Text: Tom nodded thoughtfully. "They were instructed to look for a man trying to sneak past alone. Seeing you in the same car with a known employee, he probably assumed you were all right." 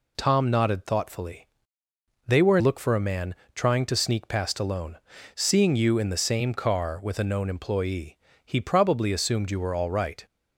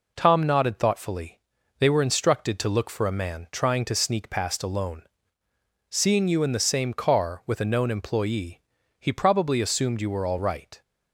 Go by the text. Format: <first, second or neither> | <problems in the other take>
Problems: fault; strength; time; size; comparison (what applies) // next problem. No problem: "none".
second | skips "instructed to"; at 2.5 s // pauses between "man" and "trying"; slight; at 3.3 s; 0.18 s long